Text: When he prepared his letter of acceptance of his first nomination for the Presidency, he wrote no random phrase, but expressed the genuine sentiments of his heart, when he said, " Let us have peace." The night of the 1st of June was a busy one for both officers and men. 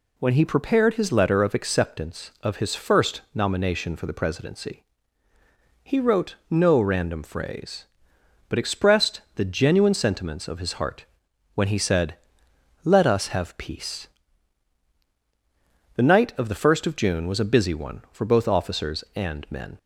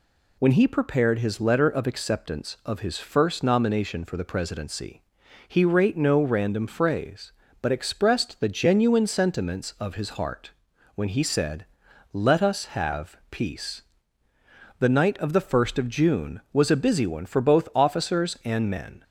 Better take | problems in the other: first | says "rate" for "wrote"; at 5.6 s

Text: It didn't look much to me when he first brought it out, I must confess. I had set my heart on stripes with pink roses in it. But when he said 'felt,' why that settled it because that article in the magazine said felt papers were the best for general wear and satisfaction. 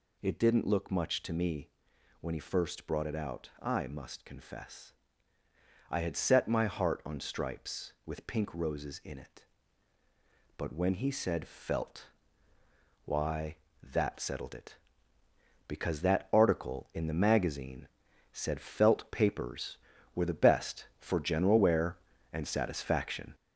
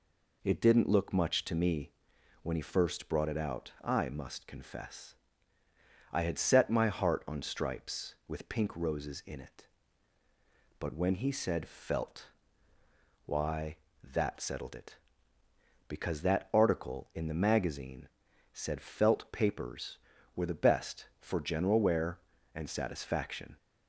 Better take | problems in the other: second | gets louder; noticeable; throughout; 4 dB // pauses between "me" and "when"; noticeable; at 1.6 s; 0.50 s long; noticeable in the second // pauses between "magazine" and "said"; noticeable; at 17.8 s; 0.46 s long; noticeable in the second

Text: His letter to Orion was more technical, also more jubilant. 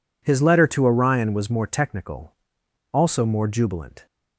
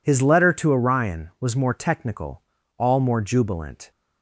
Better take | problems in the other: first | says "all" for "also"; at 2.7 s

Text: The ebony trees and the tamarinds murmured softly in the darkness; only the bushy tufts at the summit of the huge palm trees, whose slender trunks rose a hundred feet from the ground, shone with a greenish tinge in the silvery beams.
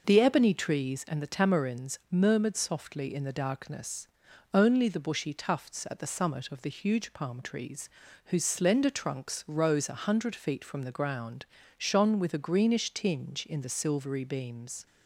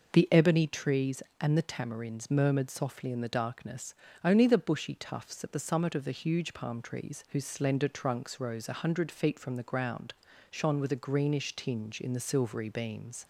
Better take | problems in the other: neither | none

